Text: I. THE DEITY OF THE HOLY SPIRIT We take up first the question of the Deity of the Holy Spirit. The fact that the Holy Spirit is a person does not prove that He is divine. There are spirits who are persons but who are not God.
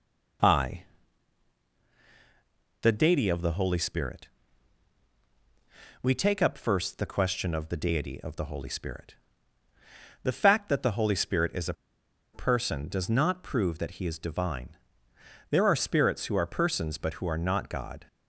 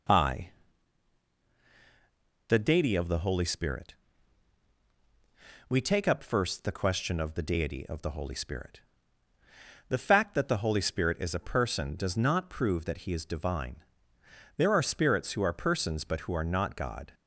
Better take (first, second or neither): second